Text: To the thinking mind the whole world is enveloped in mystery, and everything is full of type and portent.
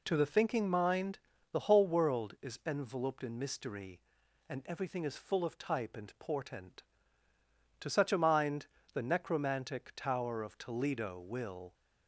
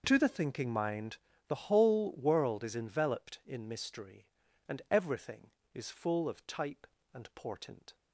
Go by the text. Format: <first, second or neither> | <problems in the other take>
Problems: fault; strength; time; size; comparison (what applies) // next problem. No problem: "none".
second | pauses between "mind" and "the"; slight; at 1.1 s; 0.32 s long; slight in the second // goes on to say "To such a mind the necromantic tower of Toledo will"; strong; from 7.7 s on; 3.9 s long